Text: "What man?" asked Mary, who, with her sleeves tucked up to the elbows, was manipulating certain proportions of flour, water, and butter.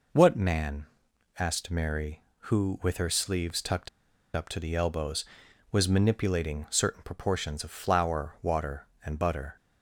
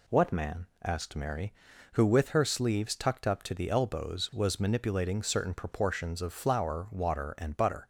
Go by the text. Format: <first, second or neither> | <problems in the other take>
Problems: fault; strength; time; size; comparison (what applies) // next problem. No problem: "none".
second | pauses between "tucked" and "up"; noticeable; at 3.8 s; 0.46 s long